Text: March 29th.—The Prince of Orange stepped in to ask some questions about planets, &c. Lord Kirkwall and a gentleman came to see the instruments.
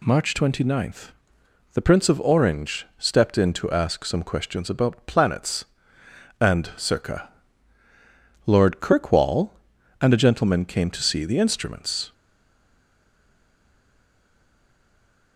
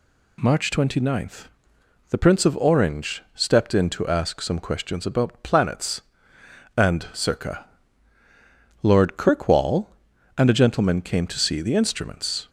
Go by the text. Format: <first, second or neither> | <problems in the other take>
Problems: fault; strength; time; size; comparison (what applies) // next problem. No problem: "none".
second | stays silent after the last word; strong; from 12.1 s on; 3.2 s long